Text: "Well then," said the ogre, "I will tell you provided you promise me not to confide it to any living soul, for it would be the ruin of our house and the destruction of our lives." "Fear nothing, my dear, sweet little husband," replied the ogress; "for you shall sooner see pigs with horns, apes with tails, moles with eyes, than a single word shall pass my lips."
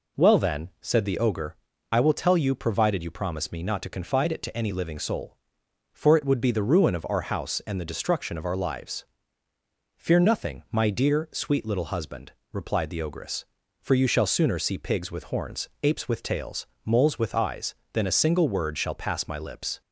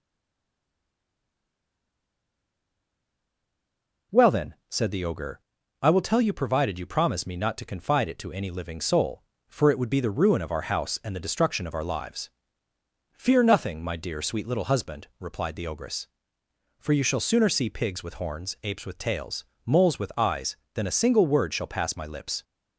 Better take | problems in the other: first | stays silent before the first word; strong; until 4.1 s; 4.1 s long

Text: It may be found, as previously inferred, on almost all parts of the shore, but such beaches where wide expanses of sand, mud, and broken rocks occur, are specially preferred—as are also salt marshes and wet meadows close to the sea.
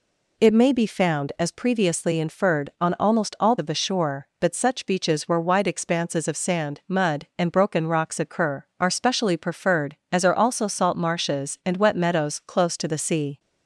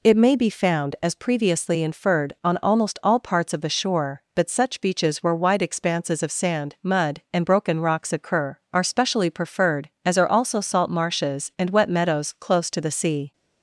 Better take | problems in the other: second | skips "parts"; at 3.5 s

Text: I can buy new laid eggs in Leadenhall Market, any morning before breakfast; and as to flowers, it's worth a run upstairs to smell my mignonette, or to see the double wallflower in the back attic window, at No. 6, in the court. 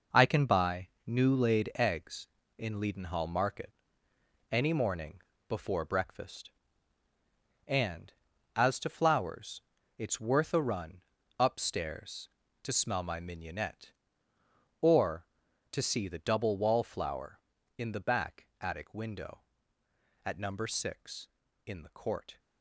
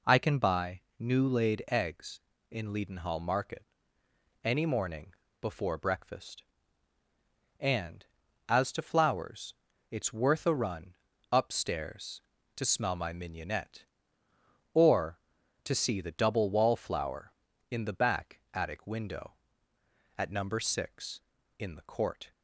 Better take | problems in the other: second | gets quieter; strong; throughout; 8.5 dB // pauses between "buy" and "new"; slight; at 0.8 s; 0.18 s long; slight in the second // pauses between "morning" and "before"; slight; at 5.2 s; 0.26 s long; slight in the second // pauses between "run" and "upstairs"; slight; at 11.0 s; 0.36 s long; slight in the second

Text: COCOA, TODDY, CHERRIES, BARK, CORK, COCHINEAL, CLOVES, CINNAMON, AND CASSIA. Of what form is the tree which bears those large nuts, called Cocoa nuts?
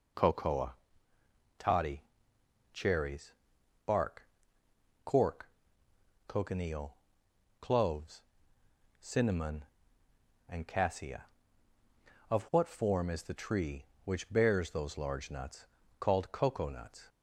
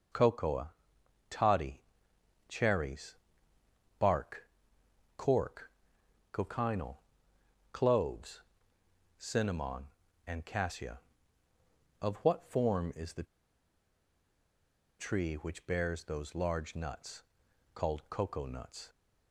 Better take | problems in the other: first | pauses between "the" and "tree"; strong; at 13.2 s; 1.7 s long

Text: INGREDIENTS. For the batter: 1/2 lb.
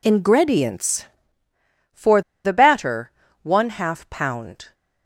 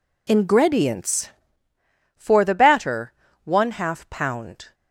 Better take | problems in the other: second | pauses between "For" and "the"; slight; at 2.2 s; 0.24 s long

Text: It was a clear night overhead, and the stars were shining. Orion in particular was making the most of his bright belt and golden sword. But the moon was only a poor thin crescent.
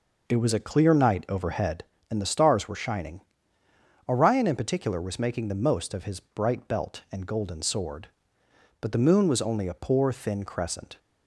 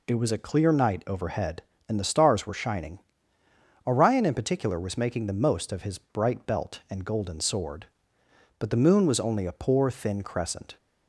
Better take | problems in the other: second | starts louder than the rest; noticeable; until 1.8 s; 5 dB

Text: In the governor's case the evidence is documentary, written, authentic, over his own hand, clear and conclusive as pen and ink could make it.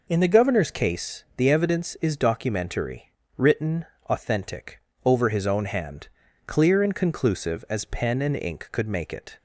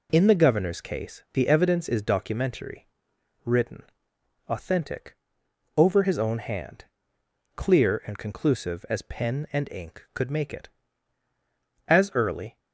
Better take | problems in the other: first | goes on to say "As early"; noticeable; from 11.8 s on; 0.72 s long

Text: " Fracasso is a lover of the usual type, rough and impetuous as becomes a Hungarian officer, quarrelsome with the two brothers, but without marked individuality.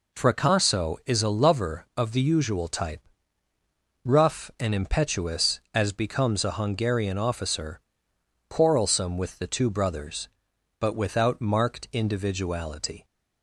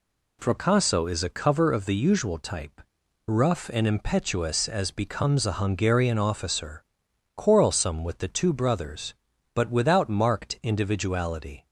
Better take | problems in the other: first | says "cover" for "lover"; at 1.2 s

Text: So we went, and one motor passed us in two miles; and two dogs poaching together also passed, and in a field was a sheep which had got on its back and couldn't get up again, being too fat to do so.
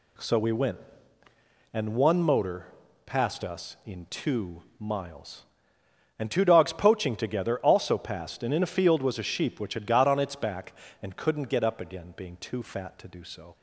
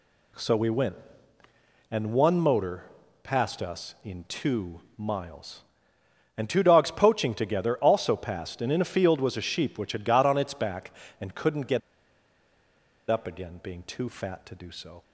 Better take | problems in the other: first | pauses between "motor" and "passed"; at 2.8 s; 0.38 s long; also in the first // pauses between "two" and "miles"; slight; at 4.8 s; 0.18 s long; slight in the first // pauses between "get" and "up"; strong; at 11.8 s; 1.3 s long

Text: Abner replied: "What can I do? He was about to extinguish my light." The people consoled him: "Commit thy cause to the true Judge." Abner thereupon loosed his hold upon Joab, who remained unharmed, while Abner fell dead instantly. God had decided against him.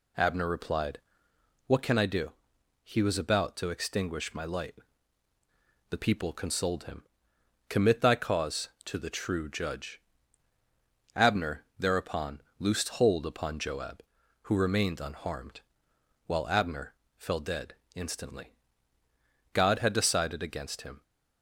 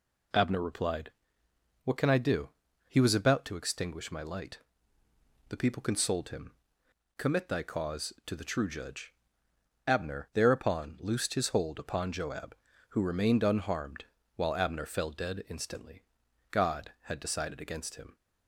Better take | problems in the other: second | pauses between "thereupon" and "loosed"; slight; at 12.4 s; 0.18 s long // skips "his"; at 12.8 s // pauses between "Abner" and "fell"; slight; at 16.9 s; 0.22 s long // pauses between "dead" and "instantly"; slight; at 17.7 s; 0.20 s long

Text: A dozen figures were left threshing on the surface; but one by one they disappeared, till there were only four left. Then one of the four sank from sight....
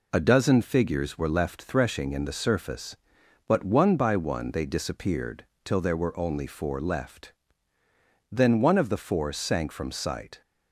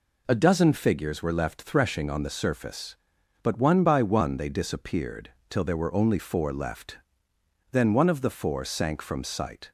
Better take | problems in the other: second | says "in" for "on"; at 2.1 s

